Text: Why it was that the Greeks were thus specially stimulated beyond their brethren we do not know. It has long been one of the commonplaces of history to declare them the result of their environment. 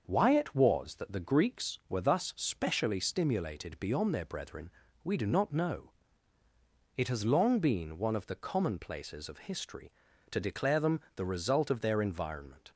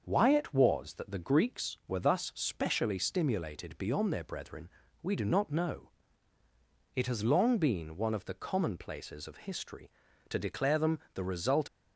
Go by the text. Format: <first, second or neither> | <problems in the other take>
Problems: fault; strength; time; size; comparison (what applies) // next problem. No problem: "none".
first | starts louder than the rest; until 1.0 s; 6.5 dB; also in the first // pauses between "brethren" and "we"; slight; at 4.6 s; 0.34 s long; slight in the first // stops before "of their environment"; at 11.6 s